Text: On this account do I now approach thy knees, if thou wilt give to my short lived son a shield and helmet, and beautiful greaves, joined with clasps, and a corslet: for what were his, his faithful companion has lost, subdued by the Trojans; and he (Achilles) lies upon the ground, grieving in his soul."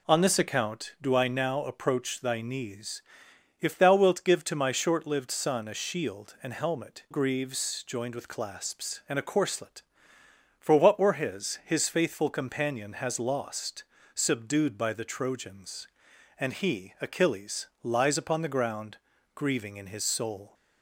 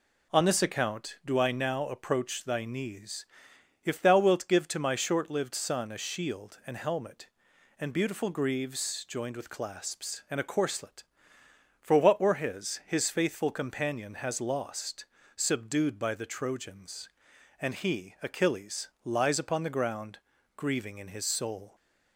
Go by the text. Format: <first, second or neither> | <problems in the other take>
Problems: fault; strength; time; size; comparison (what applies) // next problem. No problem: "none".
second | skips "and beautiful"; at 7.0 s